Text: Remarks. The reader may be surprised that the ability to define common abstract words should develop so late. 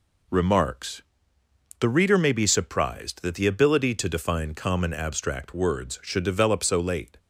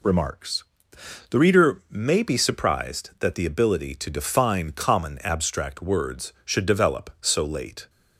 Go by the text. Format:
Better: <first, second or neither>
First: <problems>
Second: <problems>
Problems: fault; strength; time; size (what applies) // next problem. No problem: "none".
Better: neither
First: none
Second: none